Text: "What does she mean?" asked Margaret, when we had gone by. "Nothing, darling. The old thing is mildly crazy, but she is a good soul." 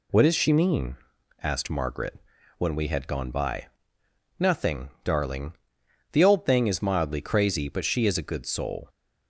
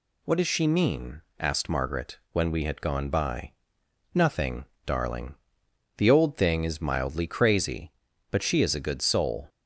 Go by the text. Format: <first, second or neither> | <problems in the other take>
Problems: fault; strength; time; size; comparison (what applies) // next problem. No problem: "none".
neither | none